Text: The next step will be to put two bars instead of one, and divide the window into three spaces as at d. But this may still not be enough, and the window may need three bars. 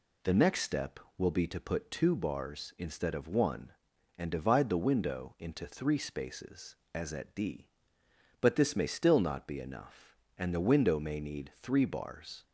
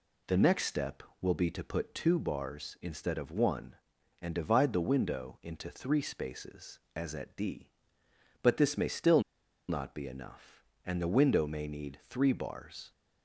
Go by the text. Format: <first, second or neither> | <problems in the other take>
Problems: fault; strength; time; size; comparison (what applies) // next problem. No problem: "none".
first | pauses between "still" and "not"; noticeable; at 9.1 s; 0.48 s long